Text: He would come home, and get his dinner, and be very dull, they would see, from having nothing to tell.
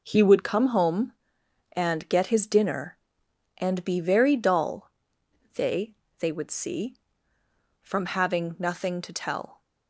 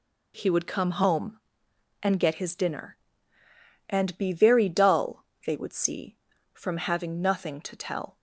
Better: second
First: says "they" twice; at 6.1 s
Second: none

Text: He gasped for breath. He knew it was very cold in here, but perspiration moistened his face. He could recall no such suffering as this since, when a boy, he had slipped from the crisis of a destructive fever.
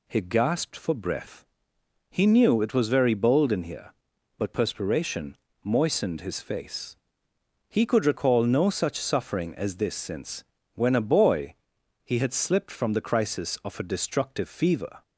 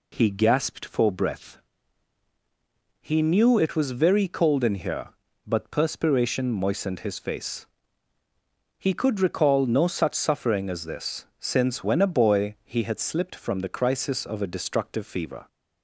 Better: second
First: says "bold" for "cold"; at 3.1 s // pauses between "perspiration" and "moistened"; slight; at 5.3 s; 0.26 s long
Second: none

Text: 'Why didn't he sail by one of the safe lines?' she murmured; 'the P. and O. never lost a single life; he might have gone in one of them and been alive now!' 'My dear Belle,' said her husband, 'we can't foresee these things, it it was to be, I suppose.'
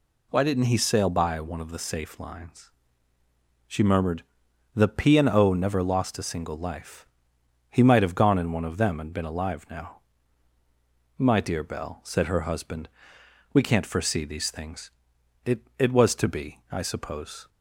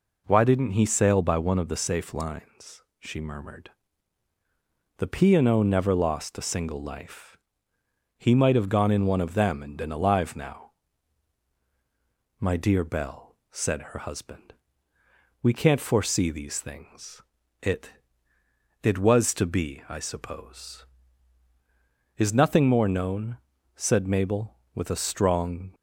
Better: first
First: none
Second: pauses between "it" and "it"; noticeable; at 17.9 s; 0.92 s long // goes on to say "Is nothing more known said Mabel with a strong"; strong; from 22.1 s on; 3.5 s long

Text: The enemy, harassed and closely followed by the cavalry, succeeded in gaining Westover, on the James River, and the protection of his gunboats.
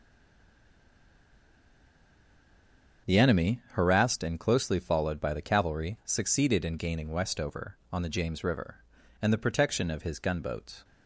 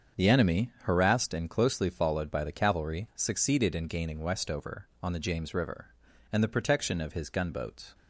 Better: second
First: stays silent before the first word; strong; until 3.0 s; 3.0 s long // starts louder than the rest; strong; until 4.1 s; 7 dB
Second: starts louder than the rest; strong; until 1.2 s; 7 dB

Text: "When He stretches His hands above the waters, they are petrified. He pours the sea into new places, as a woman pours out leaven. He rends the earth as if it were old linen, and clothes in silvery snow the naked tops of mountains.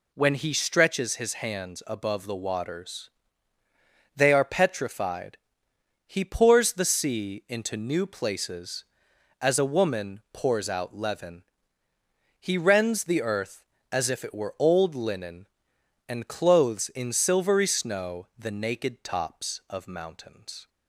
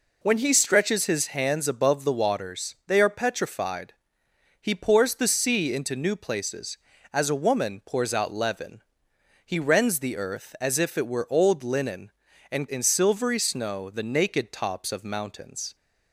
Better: first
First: none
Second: skips "clothes"; at 12.6 s

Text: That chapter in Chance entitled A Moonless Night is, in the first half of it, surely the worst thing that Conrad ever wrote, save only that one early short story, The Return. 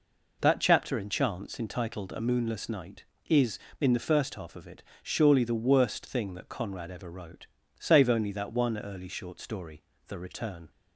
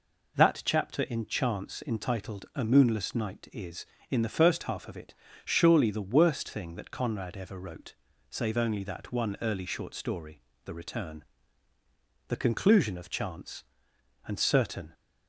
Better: first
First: none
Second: goes on to say "The conclusion of Chance and certain"; strong; from 12.2 s on; 2.6 s long

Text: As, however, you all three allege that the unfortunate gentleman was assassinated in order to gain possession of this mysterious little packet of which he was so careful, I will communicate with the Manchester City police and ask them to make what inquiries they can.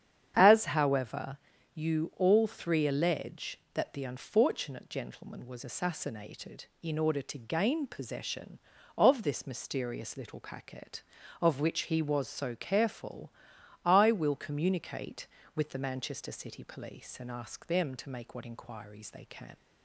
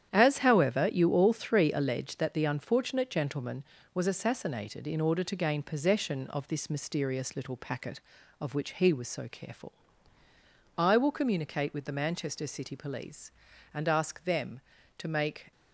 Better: first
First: starts louder than the rest; strong; until 1.3 s; 8.5 dB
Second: starts louder than the rest; strong; until 1.1 s; 10 dB // stops before "what inquiries they can"; at 15.5 s

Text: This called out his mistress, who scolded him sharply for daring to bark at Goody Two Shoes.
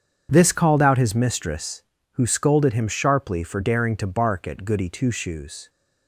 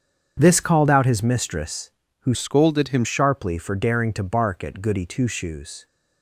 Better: first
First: starts louder than the rest; strong; until 1.3 s; 7.5 dB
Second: starts louder than the rest; strong; until 1.3 s; 7.5 dB // changes voice from "scolded" to "him"; from 2.3 to 3.0 s; 0.7 s long

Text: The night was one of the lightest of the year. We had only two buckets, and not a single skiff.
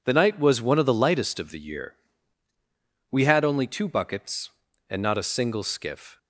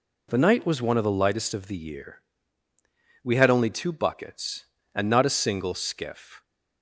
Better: neither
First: none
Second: none

